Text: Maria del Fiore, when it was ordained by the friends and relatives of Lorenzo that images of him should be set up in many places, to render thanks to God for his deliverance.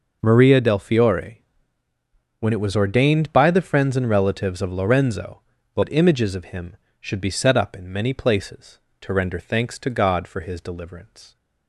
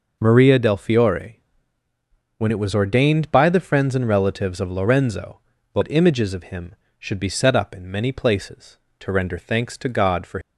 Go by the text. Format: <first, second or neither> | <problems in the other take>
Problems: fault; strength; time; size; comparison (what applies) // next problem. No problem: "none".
first | stops before "his deliverance"; at 10.4 s